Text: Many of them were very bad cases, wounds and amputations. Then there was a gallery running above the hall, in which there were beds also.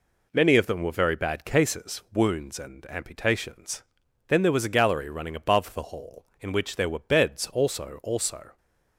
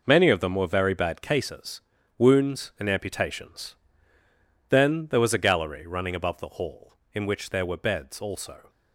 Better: second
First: says "also" twice; at 8.0 s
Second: none

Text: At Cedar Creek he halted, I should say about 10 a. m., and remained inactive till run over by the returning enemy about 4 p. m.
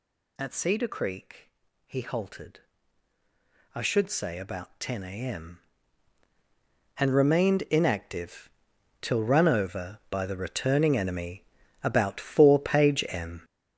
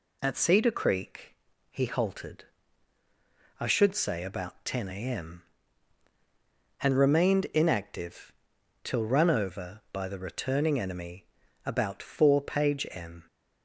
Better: second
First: gets louder; strong; throughout; 9 dB // pauses between "Creek" and "he"; at 1.4 s; 0.38 s long // pauses between "inactive" and "till"; noticeable; at 8.5 s; 0.50 s long // pauses between "enemy" and "about"; at 11.4 s; 0.40 s long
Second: pauses between "Creek" and "he"; at 1.3 s; 0.38 s long // pauses between "inactive" and "till"; noticeable; at 8.3 s; 0.49 s long // pauses between "enemy" and "about"; at 11.2 s; 0.40 s long

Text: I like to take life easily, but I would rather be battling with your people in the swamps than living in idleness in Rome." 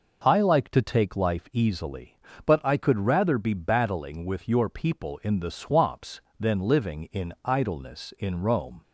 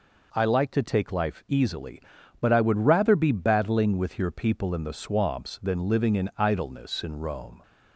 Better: second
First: says "could" for "would"; at 2.7 s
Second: none

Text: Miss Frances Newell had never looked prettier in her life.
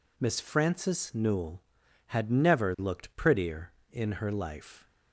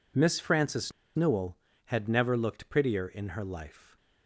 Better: first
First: none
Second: pauses between "Frances" and "Newell"; slight; at 0.9 s; 0.24 s long

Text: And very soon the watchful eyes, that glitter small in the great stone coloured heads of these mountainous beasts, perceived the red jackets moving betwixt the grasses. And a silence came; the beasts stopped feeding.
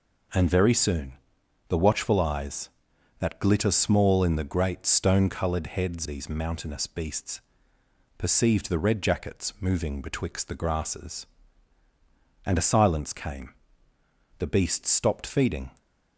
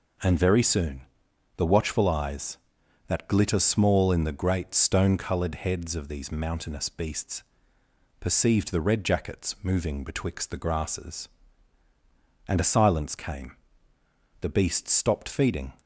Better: second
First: pauses between "soon" and "the"; noticeable; at 1.1 s; 0.54 s long // skips "of"; at 6.0 s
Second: pauses between "soon" and "the"; noticeable; at 1.0 s; 0.54 s long

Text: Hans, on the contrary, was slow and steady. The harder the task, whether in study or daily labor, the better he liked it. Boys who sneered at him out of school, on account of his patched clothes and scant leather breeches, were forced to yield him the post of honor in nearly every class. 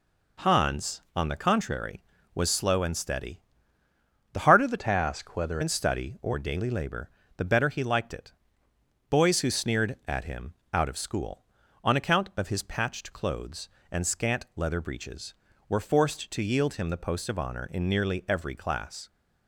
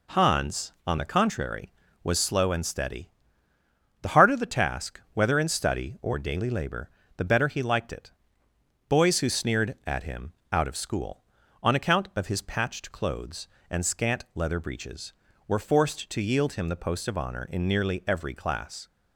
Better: second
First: changes voice from "task" to "whether"; from 4.7 to 5.5 s; 0.8 s long // pauses between "him" and "out"; slight; at 10.5 s; 0.20 s long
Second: pauses between "him" and "out"; slight; at 10.3 s; 0.20 s long

